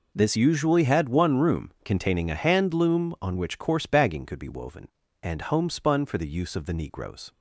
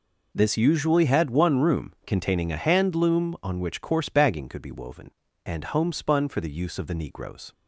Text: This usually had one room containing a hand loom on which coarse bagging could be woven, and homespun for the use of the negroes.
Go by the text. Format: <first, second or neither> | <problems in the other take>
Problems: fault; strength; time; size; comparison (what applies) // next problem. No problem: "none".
neither | none